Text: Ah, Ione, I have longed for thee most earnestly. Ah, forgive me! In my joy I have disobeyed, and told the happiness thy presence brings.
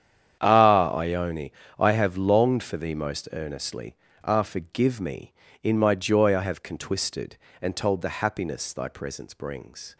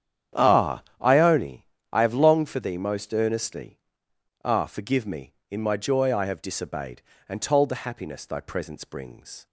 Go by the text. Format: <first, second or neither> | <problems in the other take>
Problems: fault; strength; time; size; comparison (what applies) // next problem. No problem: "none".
second | starts louder than the rest; strong; until 1.4 s; 9 dB; strong in the second // says "contwisted" for "disobeyed"; at 6.6 s